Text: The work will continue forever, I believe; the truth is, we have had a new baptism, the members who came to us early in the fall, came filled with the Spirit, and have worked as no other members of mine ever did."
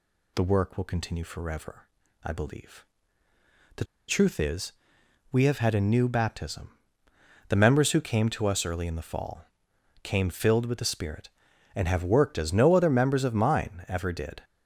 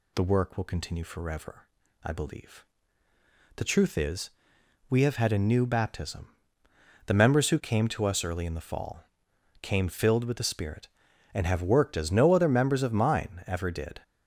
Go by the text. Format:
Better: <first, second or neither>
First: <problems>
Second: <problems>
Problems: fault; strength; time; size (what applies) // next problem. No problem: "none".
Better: second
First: pauses between "the" and "truth"; slight; at 3.8 s; 0.24 s long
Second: none